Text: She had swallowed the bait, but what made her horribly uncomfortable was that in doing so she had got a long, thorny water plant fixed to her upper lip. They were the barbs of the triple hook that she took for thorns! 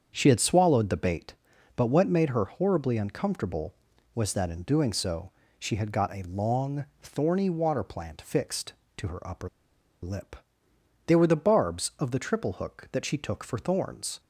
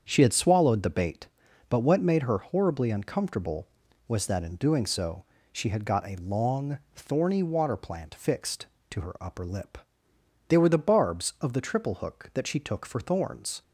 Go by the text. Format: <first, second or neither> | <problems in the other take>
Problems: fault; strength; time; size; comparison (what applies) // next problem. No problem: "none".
second | starts louder than the rest; strong; until 1.1 s; 7.5 dB; strong in the second // pauses between "so" and "she"; slight; at 5.3 s; 0.26 s long; slight in the second // pauses between "upper" and "lip"; noticeable; at 9.4 s; 0.55 s long